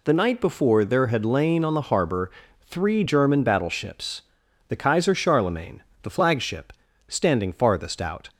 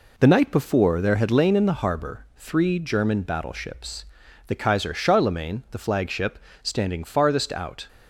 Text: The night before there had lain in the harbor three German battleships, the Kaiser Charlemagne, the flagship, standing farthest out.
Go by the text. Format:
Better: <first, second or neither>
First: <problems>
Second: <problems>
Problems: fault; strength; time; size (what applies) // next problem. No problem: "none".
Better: second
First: says "on" for "in"; at 1.6 s // pauses between "harbor" and "three"; slight; at 2.2 s; 0.32 s long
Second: none